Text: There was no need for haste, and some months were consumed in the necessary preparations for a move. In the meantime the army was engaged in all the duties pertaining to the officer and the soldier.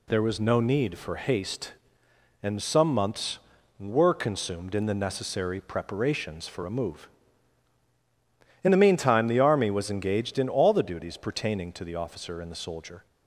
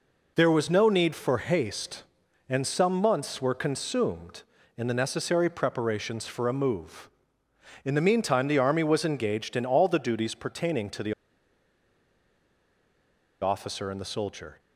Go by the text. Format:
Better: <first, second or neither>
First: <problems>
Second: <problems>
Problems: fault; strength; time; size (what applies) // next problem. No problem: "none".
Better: first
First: none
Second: pauses between "the" and "officer"; strong; at 11.1 s; 2.2 s long